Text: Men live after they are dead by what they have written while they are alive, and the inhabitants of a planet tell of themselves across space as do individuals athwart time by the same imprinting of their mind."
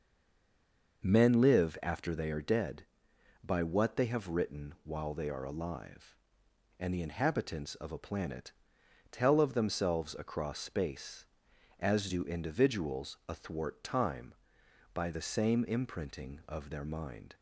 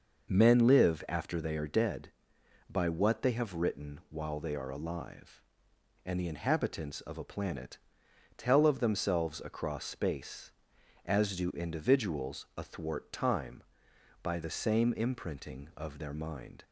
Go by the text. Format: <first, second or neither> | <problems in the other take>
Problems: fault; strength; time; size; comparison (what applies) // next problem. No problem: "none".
second | stays silent before the first word; until 1.0 s; 1.0 s long // pauses between "planet" and "tell"; noticeable; at 8.5 s; 0.58 s long; noticeable in the second